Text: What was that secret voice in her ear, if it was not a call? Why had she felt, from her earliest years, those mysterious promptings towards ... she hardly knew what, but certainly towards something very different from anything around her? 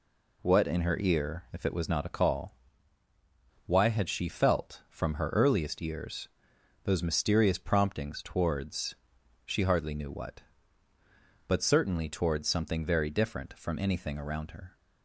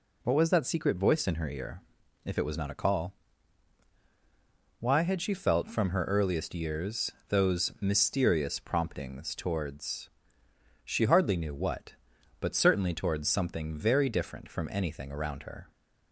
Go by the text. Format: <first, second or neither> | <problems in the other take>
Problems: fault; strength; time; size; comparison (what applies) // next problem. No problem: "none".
second | skips "was that secret voice"; at 0.6 s